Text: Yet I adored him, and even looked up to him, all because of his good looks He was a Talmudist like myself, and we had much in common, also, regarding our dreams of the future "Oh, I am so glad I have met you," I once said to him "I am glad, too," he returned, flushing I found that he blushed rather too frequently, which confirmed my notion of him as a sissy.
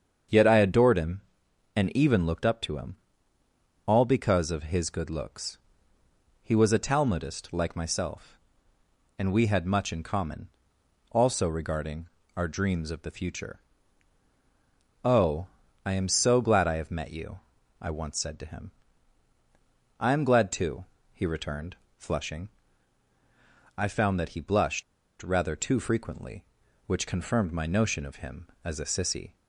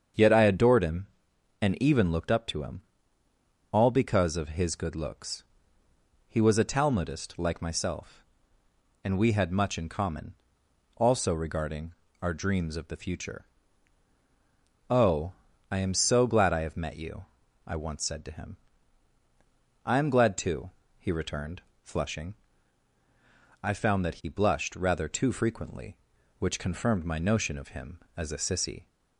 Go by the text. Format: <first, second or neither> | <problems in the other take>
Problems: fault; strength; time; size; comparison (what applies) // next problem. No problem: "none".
second | starts louder than the rest; strong; until 1.8 s; 7.5 dB; strong in the second // pauses between "looks" and "He"; noticeable; at 5.5 s; 0.86 s long; noticeable in the second // pauses between "regarding" and "our"; slight; at 12.0 s; 0.30 s long; slight in the second // pauses between "future" and "Oh"; strong; at 13.5 s; 1.4 s long; strong in the second // pauses between "him" and "I"; strong; at 18.6 s; 1.3 s long; strong in the second // pauses between "flushing" and "I"; strong; at 22.4 s; 1.2 s long; strong in the second // pauses between "blushed" and "rather"; at 24.8 s; 0.38 s long